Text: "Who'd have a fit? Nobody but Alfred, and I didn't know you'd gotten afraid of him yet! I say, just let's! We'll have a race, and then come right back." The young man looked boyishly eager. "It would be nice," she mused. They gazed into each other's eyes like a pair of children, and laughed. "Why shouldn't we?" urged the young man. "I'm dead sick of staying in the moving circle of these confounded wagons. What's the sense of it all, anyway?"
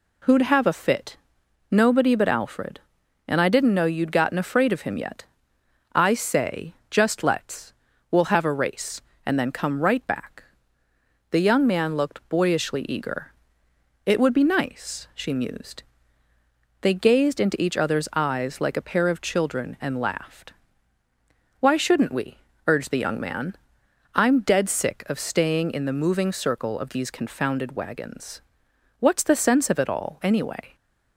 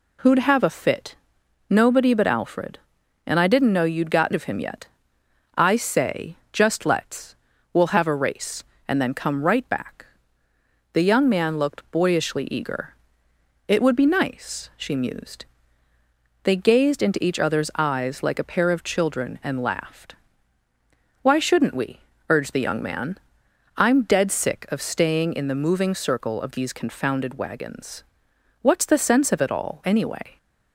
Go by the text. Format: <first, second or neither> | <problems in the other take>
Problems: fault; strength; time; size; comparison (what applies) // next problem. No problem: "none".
first | skips "afraid"; at 4.3 s